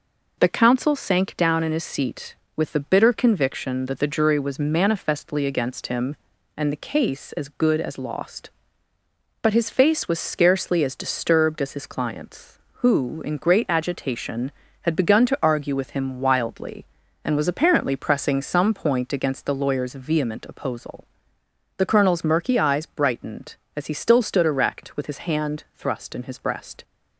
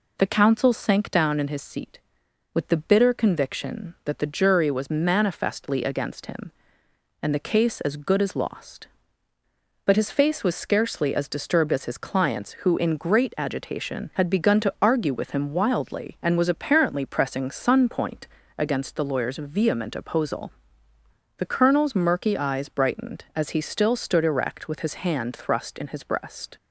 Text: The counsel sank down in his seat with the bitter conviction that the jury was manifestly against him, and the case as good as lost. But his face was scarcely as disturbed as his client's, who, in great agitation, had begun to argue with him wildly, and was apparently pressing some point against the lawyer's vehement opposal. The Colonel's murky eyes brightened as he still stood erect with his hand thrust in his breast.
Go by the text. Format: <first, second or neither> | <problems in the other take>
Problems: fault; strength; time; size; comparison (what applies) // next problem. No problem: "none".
first | says "sun" for "some"; at 17.5 s // pauses between "point" and "against"; slight; at 18.2 s; 0.30 s long